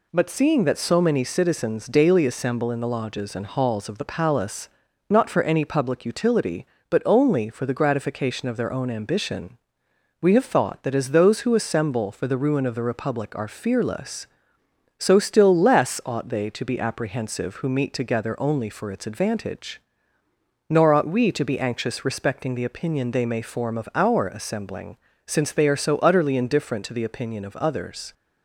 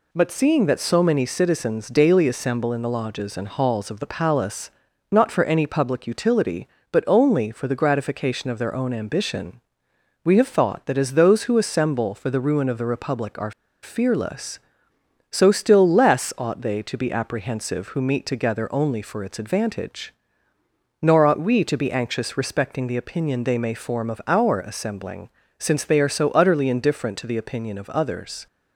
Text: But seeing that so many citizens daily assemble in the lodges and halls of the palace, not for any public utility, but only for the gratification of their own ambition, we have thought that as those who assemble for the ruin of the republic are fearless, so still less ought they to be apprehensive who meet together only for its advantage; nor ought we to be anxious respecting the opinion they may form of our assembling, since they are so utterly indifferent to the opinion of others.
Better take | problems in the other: first | pauses between "are" and "fearless"; slight; at 13.5 s; 0.31 s long

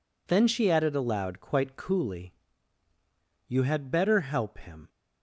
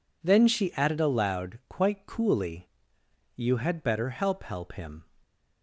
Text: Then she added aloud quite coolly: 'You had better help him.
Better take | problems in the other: first | says "help" twice; at 4.4 s

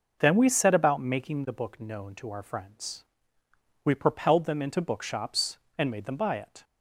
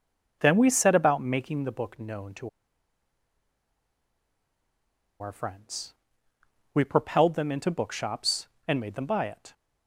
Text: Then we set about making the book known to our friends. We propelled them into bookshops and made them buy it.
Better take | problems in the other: first | pauses between "to" and "our"; strong; at 2.4 s; 2.7 s long

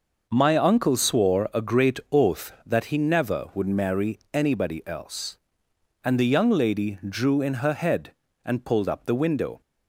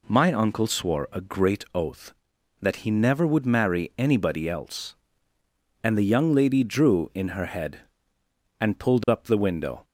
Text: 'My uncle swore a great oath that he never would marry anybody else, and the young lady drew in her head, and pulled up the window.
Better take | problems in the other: neither | none

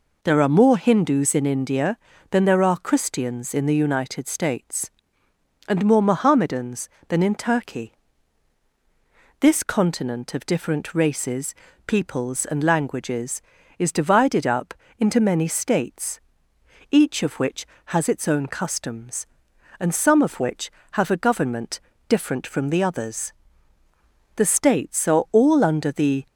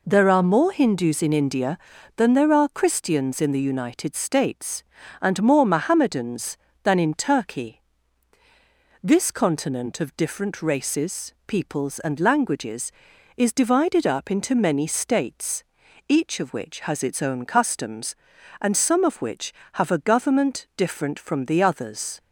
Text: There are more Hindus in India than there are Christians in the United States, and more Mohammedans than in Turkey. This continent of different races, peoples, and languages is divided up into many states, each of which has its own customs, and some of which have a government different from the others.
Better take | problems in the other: second | pauses between "up" and "into"; slight; at 14.7 s; 0.24 s long // pauses between "government" and "different"; slight; at 21.7 s; 0.30 s long // goes on to say "The states are all under the"; strong; from 24.3 s on; 1.9 s long

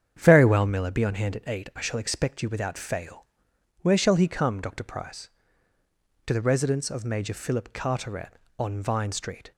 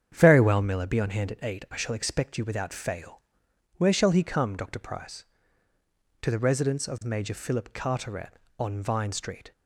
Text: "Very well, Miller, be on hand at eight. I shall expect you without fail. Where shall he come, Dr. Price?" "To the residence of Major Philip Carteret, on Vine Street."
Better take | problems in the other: neither | starts louder than the rest; strong; the same in both

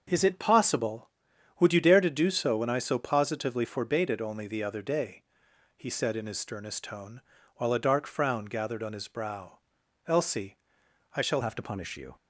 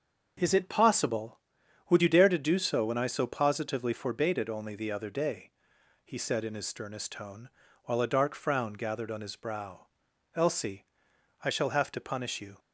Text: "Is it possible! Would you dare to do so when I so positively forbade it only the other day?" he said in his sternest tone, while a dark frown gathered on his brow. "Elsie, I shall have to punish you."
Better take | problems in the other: second | starts louder than the rest; until 1.1 s; 6.5 dB; also in the second // changes voice at "have"; from 11.4 s on; 0.7 s long

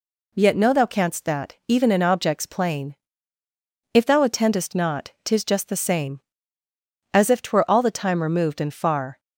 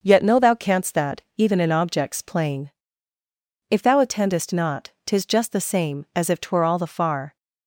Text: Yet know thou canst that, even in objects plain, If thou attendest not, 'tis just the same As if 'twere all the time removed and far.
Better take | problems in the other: first | starts louder than the rest; until 1.0 s; 6 dB // skips "time removed and"; at 6.8 s

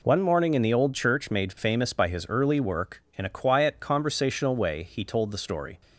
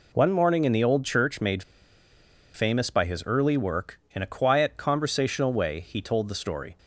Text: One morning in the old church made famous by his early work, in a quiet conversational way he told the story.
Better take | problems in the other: first | pauses between "made" and "famous"; noticeable; at 1.6 s; 0.90 s long

